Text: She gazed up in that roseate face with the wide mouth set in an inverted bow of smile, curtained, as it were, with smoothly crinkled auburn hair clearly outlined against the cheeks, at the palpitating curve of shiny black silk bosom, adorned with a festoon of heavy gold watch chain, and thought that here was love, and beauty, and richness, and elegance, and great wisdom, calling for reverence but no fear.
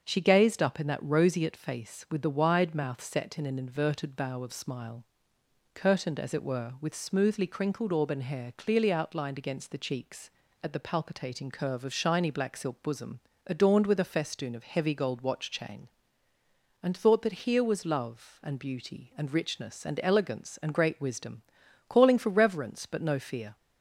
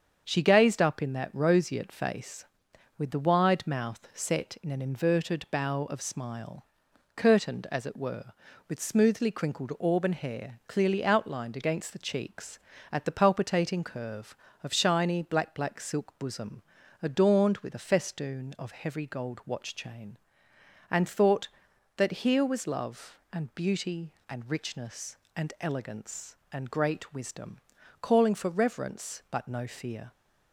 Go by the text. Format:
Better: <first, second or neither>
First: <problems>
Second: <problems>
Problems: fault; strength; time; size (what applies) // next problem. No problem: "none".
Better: first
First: starts louder than the rest; until 1.0 s; 6.5 dB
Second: starts louder than the rest; until 1.2 s; 7 dB // says "black" twice; at 15.5 s